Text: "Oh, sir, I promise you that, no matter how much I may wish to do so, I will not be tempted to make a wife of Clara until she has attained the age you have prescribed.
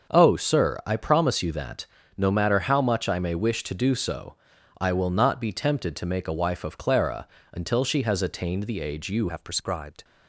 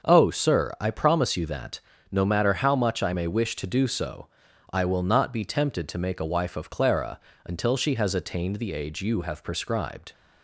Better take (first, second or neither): second